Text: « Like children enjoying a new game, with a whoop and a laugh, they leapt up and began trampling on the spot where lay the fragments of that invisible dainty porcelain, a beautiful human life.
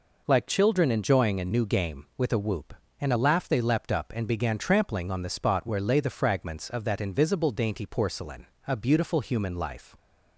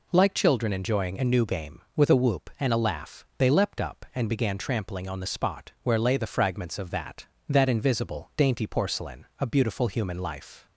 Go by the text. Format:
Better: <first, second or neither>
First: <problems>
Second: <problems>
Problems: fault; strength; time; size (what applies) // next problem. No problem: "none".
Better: first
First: none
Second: says "that" twice; at 7.4 s